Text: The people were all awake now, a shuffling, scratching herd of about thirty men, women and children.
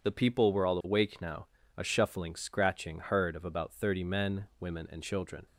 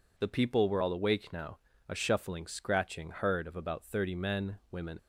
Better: first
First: none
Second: stops before "and children"; at 4.9 s

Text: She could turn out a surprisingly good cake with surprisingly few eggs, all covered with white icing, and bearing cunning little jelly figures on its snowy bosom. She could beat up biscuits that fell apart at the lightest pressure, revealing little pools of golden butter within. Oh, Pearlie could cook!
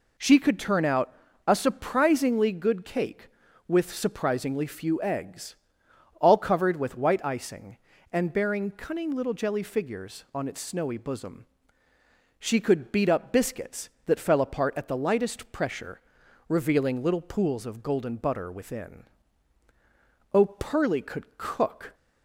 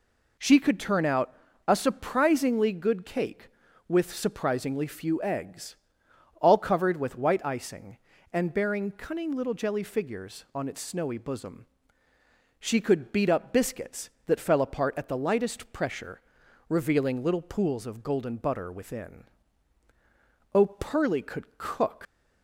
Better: first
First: pauses between "out" and "a"; slight; at 1.1 s; 0.32 s long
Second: pauses between "out" and "a"; slight; at 1.3 s; 0.32 s long // leaves "cook" unfinished; at 22.0 s; 95 ms

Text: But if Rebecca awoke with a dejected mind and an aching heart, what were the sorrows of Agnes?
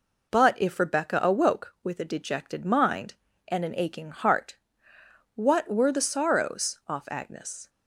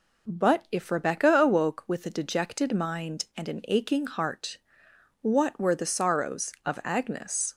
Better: second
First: says "off" for "of"; at 6.8 s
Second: none

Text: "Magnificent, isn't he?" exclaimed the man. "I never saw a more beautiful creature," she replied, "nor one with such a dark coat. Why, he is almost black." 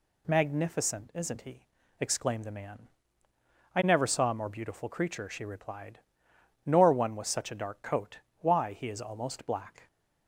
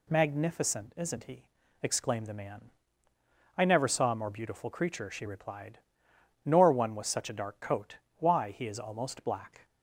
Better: neither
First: none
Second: none

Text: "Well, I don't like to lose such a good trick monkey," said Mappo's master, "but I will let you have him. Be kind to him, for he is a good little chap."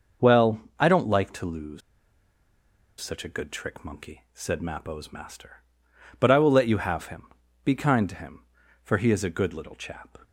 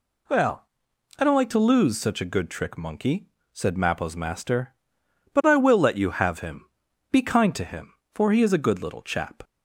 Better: second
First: pauses between "lose" and "such"; at 1.8 s; 1.2 s long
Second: none

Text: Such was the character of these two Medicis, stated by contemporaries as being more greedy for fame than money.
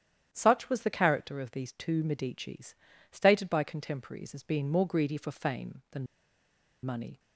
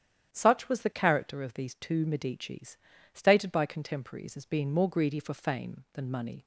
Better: second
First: starts louder than the rest; strong; until 1.3 s; 10 dB // pauses between "than" and "money"; noticeable; at 6.0 s; 0.79 s long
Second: starts louder than the rest; strong; until 1.3 s; 10 dB

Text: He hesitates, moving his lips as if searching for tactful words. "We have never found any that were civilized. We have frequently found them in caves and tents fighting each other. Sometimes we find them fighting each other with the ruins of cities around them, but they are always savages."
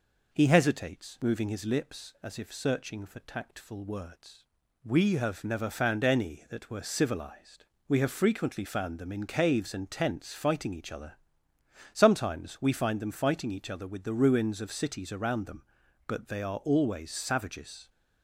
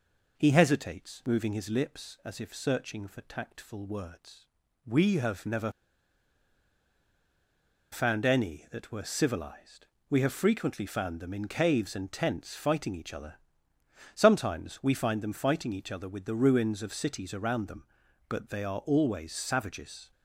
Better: first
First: none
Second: pauses between "never" and "found"; strong; at 5.7 s; 2.2 s long

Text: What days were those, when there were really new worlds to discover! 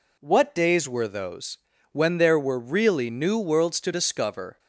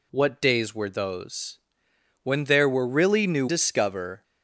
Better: first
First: none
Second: skips "worlds to"; at 3.4 s

